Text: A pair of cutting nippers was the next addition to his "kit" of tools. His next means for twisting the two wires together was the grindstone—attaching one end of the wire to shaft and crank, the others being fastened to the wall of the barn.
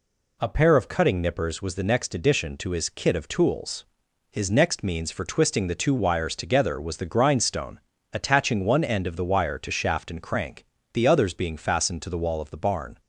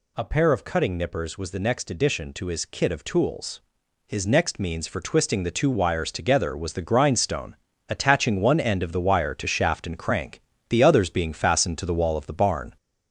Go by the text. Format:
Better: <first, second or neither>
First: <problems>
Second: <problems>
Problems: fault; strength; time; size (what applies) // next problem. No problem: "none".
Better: first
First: none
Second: gets louder; slight; throughout; 3 dB